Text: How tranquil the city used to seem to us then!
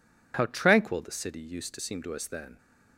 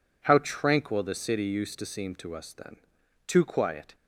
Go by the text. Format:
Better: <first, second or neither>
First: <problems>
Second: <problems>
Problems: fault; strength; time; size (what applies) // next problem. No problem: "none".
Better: first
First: none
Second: goes on to say "Too quiet"; noticeable; from 3.2 s on; 0.68 s long